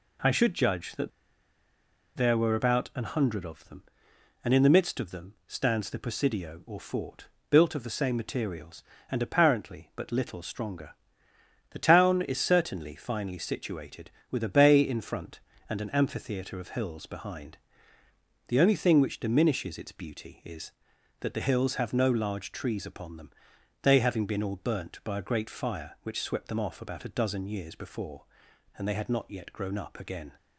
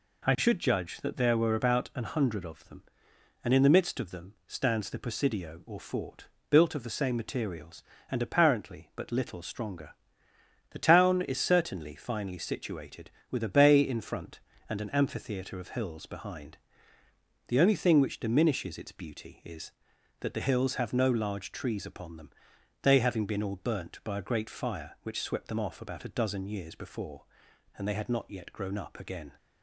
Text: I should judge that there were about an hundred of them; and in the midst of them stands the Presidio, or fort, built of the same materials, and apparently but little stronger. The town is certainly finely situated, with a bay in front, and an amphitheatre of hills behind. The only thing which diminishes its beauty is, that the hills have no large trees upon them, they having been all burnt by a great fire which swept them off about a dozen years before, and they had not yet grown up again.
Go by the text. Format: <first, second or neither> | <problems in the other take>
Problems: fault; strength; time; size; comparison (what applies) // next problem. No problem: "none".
second | pauses between "that" and "there"; at 1.1 s; 1.0 s long